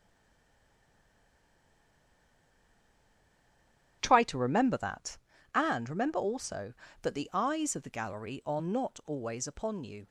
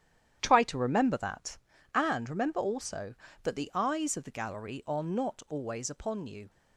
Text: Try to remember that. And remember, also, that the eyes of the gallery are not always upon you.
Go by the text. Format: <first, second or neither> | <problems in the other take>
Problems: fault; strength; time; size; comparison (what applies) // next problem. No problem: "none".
second | stays silent before the first word; strong; until 4.0 s; 4.0 s long // starts louder than the rest; strong; until 5.0 s; 10.5 dB; strong in the second